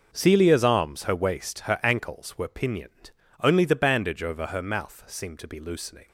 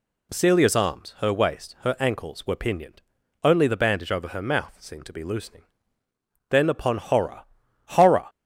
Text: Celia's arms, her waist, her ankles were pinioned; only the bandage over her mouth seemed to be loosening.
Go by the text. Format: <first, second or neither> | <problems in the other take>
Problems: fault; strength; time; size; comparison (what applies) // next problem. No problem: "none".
first | goes on to say "Then upon horror horror"; strong; from 6.4 s on; 1.8 s long